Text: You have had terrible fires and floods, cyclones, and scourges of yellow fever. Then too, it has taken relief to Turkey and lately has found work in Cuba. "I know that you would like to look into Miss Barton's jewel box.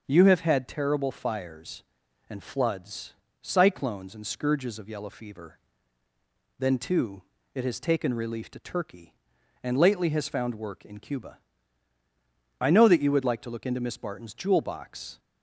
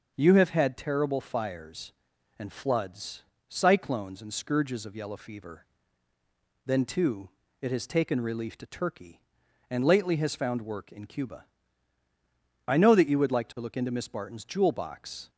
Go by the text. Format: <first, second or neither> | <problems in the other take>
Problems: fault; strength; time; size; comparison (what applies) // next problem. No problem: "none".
neither | starts louder than the rest; the same in both